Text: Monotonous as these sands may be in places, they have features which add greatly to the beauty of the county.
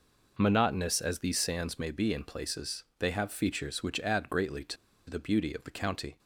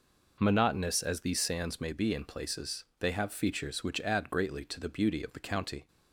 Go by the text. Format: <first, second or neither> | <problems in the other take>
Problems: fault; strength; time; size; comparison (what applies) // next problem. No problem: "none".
second | pauses between "to" and "the"; slight; at 4.7 s; 0.32 s long